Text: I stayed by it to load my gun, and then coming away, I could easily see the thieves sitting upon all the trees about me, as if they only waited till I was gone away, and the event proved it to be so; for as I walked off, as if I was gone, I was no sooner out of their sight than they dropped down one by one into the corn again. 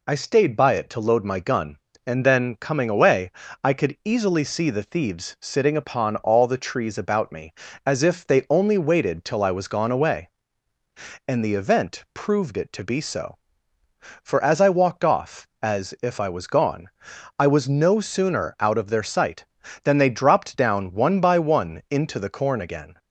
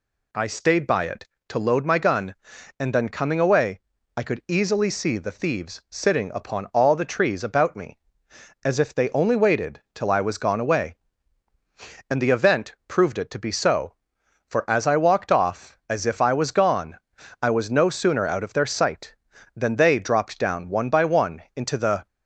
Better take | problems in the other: first | stops before "corn again"; at 22.0 s

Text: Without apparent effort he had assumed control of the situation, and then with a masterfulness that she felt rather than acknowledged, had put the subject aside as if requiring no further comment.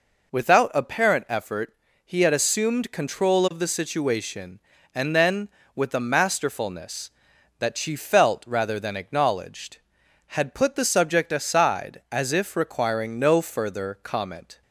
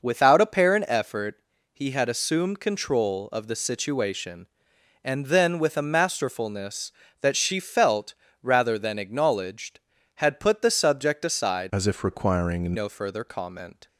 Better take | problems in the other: first | pauses between "effort" and "he"; at 1.3 s; 0.38 s long; slight in the first // pauses between "felt" and "rather"; slight; at 8.1 s; 0.28 s long // changes voice from "as" to "requiring"; from 11.7 to 12.7 s; 1.0 s long

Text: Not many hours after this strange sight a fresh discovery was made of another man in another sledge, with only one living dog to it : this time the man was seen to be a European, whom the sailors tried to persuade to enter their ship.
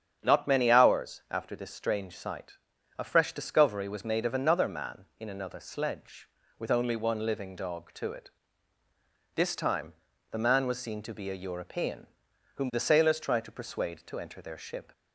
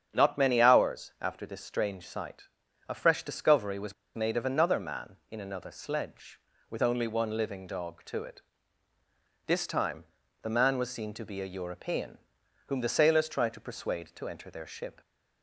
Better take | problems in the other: first | starts louder than the rest; strong; until 1.1 s; 8 dB; strong in the first // pauses between "sight" and "a"; at 2.4 s; 0.40 s long; also in the first // pauses between "was" and "made"; slight; at 3.9 s; 0.20 s long // pauses between "time" and "the"; slight; at 10.0 s; 0.36 s long; slight in the first

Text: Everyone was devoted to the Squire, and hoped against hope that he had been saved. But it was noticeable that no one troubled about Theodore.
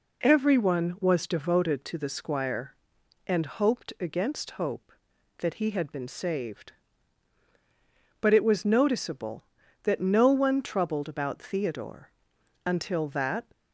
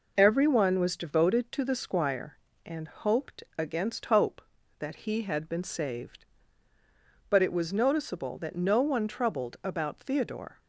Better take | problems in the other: second | goes on to say "Until that"; noticeable; from 12.6 s on; 0.82 s long

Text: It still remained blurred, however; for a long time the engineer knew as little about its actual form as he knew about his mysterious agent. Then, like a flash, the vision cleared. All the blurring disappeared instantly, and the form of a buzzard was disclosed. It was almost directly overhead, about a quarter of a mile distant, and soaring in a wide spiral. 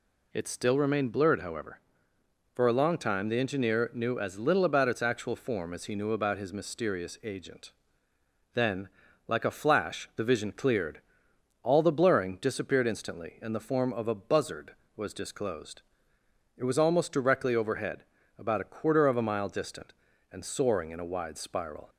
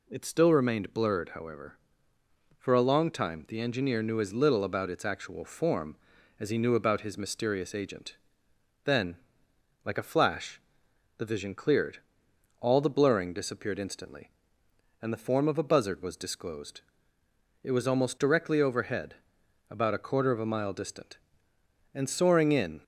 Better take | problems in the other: first | stops before "a wide spiral"; at 22.8 s

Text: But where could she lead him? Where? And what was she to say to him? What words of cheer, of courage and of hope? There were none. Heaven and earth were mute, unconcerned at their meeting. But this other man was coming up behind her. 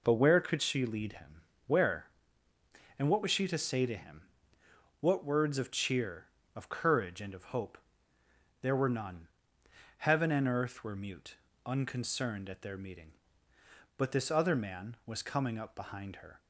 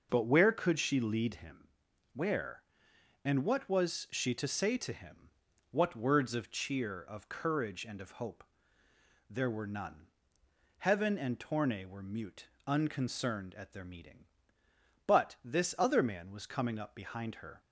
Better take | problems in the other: first | says "torne" for "earth"; at 11.3 s

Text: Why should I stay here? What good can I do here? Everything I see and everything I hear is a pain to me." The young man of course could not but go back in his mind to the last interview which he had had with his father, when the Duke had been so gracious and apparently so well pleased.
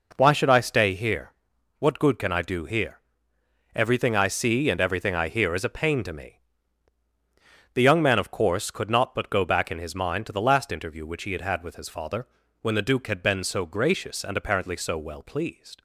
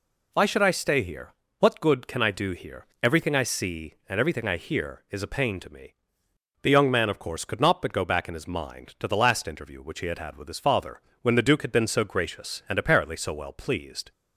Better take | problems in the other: neither | none

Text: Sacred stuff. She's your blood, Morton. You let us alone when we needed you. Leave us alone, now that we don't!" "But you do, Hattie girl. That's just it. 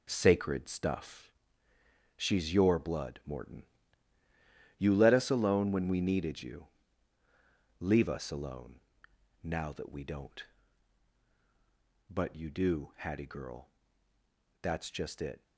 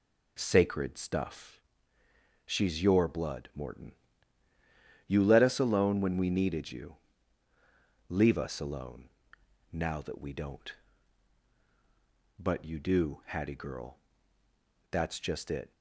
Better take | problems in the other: second | gets quieter; strong; throughout; 8 dB

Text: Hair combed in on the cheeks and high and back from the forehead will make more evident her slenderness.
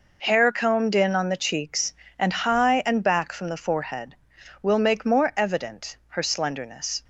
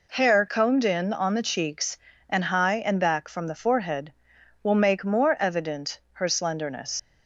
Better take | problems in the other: first | leaves "slenderness" unfinished; at 6.9 s; 75 ms

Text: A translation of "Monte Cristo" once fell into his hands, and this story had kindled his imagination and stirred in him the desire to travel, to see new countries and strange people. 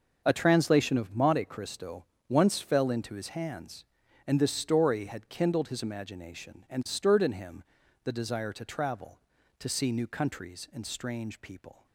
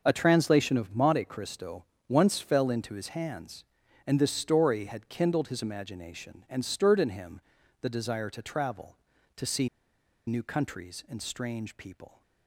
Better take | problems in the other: first | starts louder than the rest; noticeable; until 1.0 s; 6 dB; noticeable in the first // pauses between "Cristo" and "once"; slight; at 1.8 s; 0.24 s long; slight in the first // pauses between "him" and "the"; at 7.3 s; 0.44 s long; also in the first // pauses between "see" and "new"; noticeable; at 9.6 s; 0.59 s long

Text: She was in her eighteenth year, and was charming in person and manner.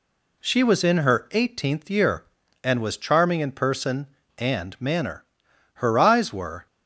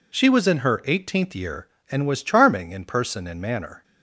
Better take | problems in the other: second | goes on to say "Her eyes were"; noticeable; from 5.7 s on; 0.92 s long

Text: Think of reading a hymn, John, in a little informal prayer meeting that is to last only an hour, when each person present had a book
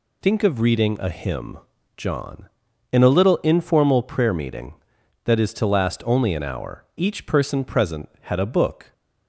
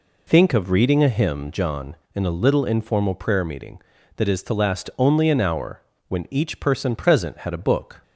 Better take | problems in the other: second | skips "when"; at 6.9 s

